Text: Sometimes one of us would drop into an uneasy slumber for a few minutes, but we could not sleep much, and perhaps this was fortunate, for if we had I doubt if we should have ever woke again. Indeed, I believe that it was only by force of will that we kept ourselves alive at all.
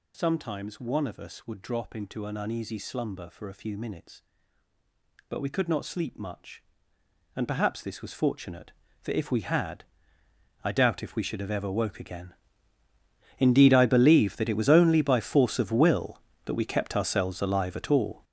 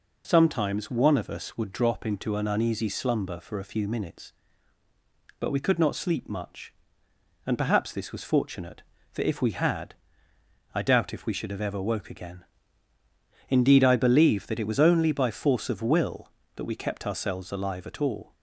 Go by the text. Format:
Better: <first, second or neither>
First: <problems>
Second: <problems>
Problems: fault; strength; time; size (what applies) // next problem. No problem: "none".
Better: second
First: gets louder; strong; throughout; 10.5 dB // pauses between "had" and "I"; noticeable; at 9.8 s; 0.80 s long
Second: pauses between "had" and "I"; noticeable; at 9.9 s; 0.80 s long